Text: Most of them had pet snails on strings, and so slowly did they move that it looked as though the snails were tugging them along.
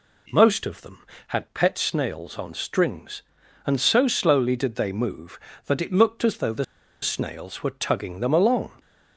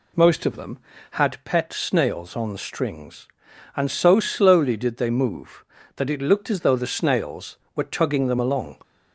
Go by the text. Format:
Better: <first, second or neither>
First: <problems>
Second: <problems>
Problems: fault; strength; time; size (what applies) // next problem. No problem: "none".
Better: second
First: pauses between "the" and "snails"; at 6.6 s; 0.37 s long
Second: none